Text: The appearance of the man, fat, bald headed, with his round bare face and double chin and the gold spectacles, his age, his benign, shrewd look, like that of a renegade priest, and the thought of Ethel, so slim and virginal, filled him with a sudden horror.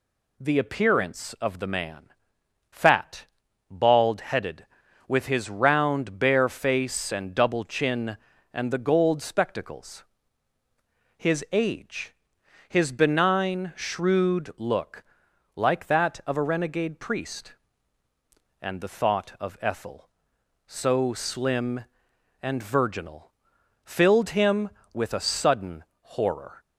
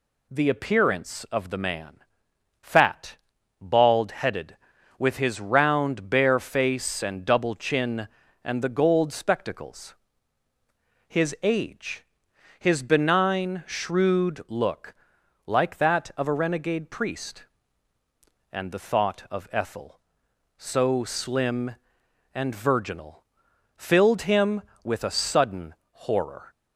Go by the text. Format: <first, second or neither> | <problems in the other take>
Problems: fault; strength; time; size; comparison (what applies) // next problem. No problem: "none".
neither | pauses between "sudden" and "horror"; slight; the same in both